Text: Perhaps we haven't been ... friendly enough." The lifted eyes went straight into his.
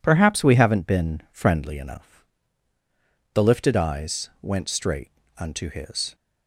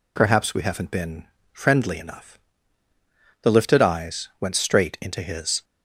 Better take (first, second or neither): second